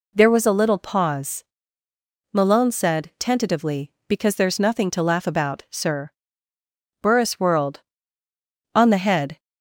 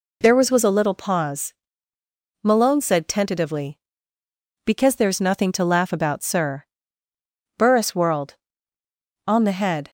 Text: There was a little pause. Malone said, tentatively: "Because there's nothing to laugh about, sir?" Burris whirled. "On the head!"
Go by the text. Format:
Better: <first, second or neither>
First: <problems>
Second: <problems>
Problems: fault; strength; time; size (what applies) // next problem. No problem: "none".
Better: first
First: none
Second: says "was" twice; at 0.5 s